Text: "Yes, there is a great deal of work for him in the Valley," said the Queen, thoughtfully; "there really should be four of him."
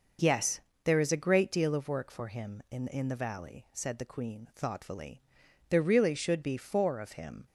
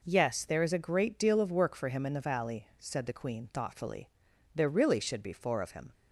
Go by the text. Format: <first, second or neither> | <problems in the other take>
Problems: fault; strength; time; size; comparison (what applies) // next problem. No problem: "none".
second | says "in" twice; at 2.8 s